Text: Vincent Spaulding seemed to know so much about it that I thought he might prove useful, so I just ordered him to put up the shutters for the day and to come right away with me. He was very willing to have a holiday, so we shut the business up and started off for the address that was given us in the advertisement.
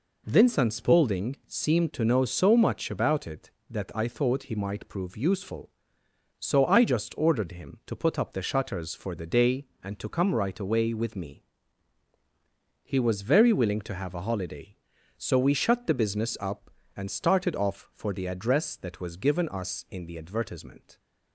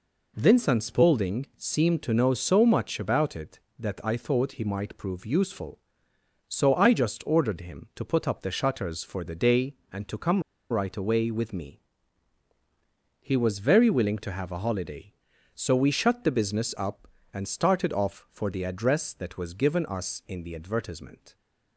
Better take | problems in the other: first | pauses between "come" and "right"; slight; at 10.4 s; 0.28 s long

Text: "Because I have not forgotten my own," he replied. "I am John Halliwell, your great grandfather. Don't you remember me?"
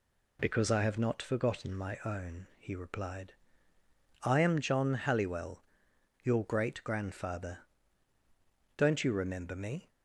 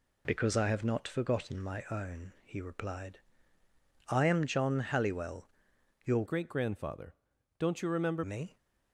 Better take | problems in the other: first | changes voice from "great" to "remember"; from 6.2 to 8.2 s; 2.0 s long

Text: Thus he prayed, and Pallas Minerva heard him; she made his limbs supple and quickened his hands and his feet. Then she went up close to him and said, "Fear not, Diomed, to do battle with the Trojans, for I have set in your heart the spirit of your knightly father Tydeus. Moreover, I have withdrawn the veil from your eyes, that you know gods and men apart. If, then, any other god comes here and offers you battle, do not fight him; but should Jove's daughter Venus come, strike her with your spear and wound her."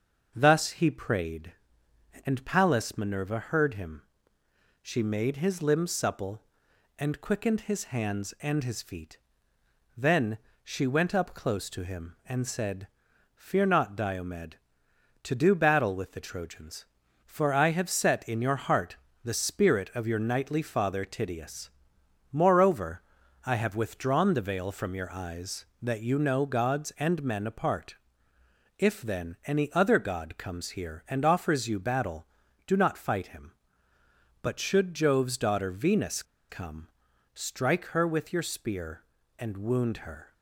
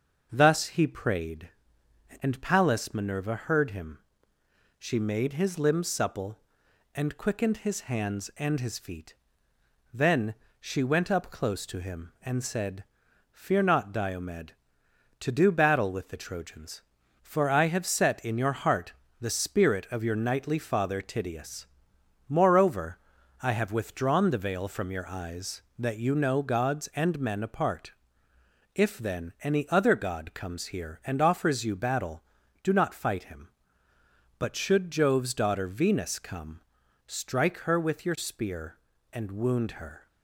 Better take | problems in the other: second | starts louder than the rest; noticeable; until 1.3 s; 6 dB; noticeable in the second // pauses between "Then" and "she"; slight; at 10.3 s; 0.26 s long; slight in the second // pauses between "heart" and "the"; slight; at 18.9 s; 0.26 s long; slight in the second // pauses between "Venus" and "come"; slight; at 36.2 s; 0.26 s long

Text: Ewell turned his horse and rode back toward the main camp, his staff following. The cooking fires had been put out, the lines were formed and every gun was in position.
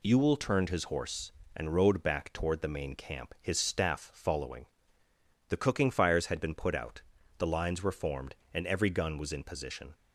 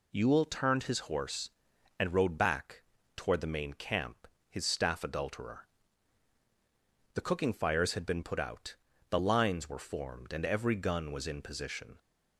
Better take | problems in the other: first | pauses between "back" and "toward"; slight; at 2.8 s; 0.34 s long // says "adulterer" for "following"; at 5.0 s

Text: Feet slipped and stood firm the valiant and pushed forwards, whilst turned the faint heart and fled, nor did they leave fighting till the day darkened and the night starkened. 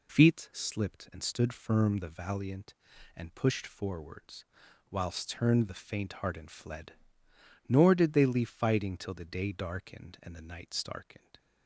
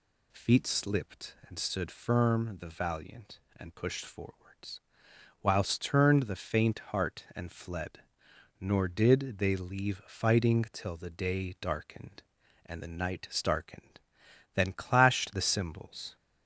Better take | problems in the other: first | goes on to say "Then clashed the cymbals"; from 14.5 s on; 1.6 s long

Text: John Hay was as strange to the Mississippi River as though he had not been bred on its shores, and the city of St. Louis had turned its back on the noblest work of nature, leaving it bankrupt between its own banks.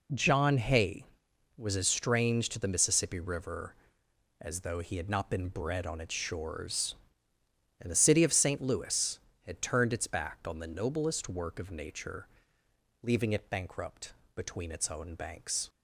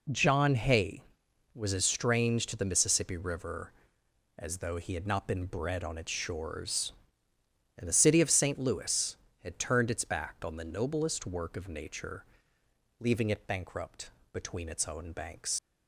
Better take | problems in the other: first | pauses between "bankrupt" and "between"; slight; at 14.0 s; 0.24 s long; slight in the first // leaves "banks" unfinished; at 15.5 s; 75 ms

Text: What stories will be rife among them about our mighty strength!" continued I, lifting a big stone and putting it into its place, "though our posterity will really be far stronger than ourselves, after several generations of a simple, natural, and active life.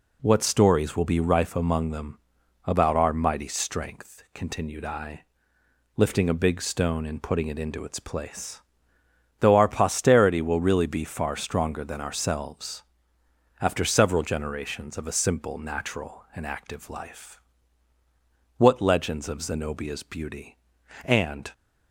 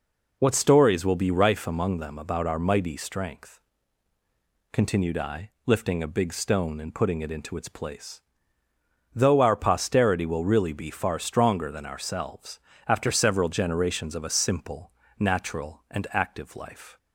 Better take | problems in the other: second | pauses between "them" and "about"; noticeable; at 2.1 s; 0.46 s long // goes on to say "What legends of Zenobia's beauty and"; strong; from 18.5 s on; 2.9 s long

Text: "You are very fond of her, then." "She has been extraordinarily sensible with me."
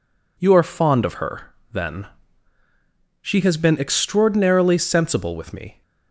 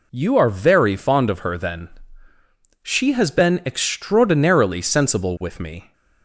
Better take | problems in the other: second | skips "very"; at 0.6 s

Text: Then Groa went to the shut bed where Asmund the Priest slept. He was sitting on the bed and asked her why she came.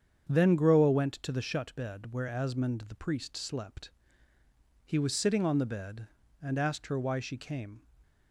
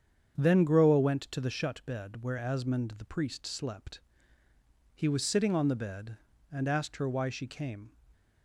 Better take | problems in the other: neither | starts louder than the rest; strong; the same in both

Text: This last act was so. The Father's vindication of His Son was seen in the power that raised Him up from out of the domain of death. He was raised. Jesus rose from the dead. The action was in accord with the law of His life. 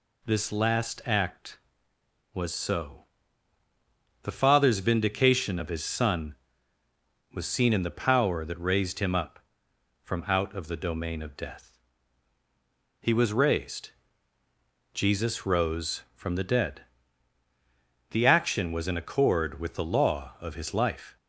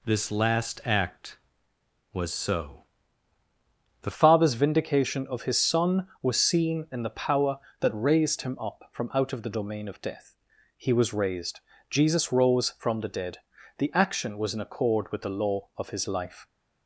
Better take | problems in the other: first | changes voice at "Father's"; from 4.1 s on; 12.3 s long

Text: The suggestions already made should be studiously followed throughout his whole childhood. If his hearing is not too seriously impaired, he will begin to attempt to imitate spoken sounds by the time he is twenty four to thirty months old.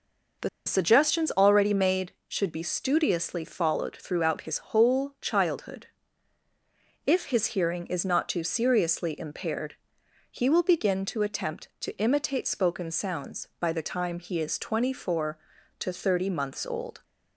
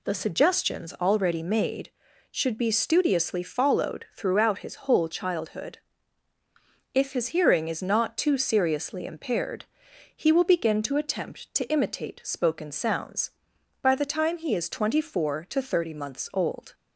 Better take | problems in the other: second | pauses between "The" and "suggestions"; slight; at 0.4 s; 0.17 s long

